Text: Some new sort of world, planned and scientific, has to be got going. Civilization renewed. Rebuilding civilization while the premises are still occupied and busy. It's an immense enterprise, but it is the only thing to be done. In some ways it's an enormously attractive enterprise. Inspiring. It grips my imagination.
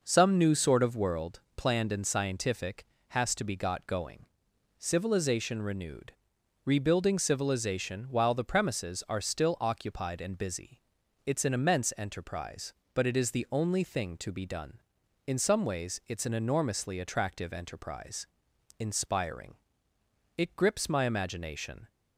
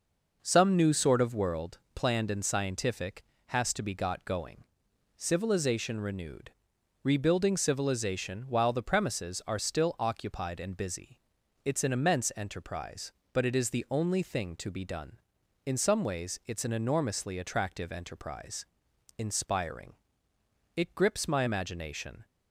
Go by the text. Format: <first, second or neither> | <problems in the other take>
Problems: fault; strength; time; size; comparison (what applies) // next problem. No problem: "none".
neither | none